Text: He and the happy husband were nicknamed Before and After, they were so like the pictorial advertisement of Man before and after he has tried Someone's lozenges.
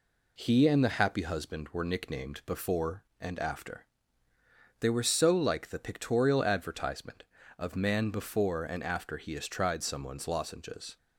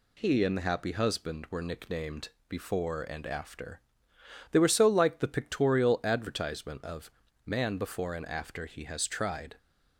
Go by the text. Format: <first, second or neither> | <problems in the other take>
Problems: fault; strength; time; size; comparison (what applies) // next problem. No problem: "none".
first | pauses between "nicknamed" and "Before"; slight; at 2.2 s; 0.18 s long // pauses between "of" and "Man"; slight; at 7.1 s; 0.34 s long // stops before "Someone's lozenges"; at 9.5 s